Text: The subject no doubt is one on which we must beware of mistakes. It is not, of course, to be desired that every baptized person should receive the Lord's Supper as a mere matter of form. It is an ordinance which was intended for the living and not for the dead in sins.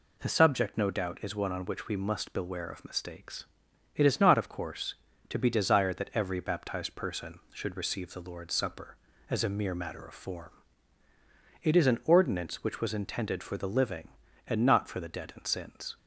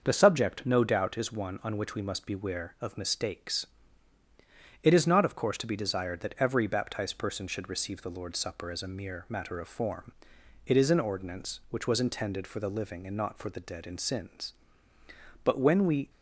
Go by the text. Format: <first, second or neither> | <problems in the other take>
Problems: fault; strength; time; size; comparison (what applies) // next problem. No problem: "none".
first | starts louder than the rest; until 1.0 s; 6 dB // goes on to say "But when we"; noticeable; from 15.4 s on; 0.66 s long